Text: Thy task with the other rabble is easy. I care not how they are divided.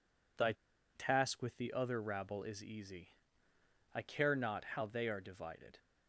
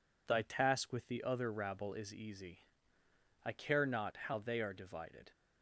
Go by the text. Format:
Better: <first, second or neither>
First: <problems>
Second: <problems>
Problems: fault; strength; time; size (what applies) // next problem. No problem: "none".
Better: second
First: pauses between "Thy" and "task"; at 0.5 s; 0.42 s long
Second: none